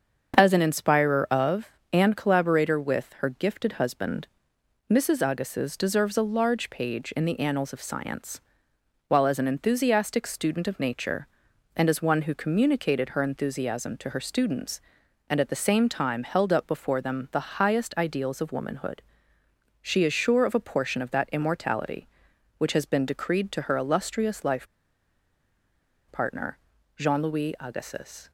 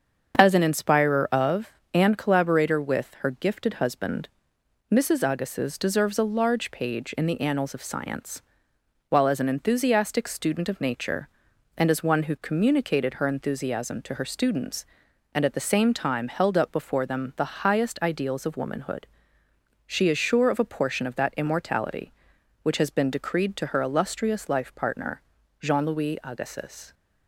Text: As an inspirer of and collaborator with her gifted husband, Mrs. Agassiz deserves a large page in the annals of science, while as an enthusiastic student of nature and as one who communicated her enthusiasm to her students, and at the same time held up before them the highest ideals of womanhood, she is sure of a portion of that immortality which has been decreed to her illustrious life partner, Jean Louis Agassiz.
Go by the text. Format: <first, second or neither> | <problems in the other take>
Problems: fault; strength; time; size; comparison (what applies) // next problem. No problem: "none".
second | starts louder than the rest; until 1.3 s; 7 dB; also in the second // pauses between "life" and "partner"; strong; at 24.6 s; 1.4 s long